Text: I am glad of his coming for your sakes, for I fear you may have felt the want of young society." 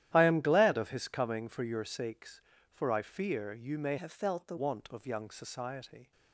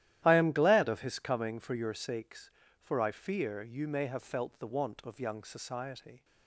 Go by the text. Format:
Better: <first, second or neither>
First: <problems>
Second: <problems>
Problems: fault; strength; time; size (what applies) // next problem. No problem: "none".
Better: second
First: starts louder than the rest; strong; until 1.1 s; 12 dB // changes voice from "have" to "the"; from 3.9 to 4.5 s; 0.6 s long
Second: starts louder than the rest; strong; until 1.2 s; 12.5 dB